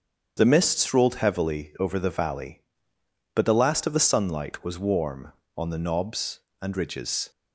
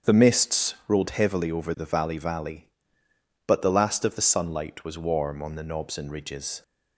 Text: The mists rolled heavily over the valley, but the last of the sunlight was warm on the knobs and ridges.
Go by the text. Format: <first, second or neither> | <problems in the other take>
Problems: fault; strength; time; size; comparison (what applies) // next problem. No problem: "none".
first | starts louder than the rest; strong; until 1.1 s; 7 dB; strong in the first // says "valley" twice; at 2.1 s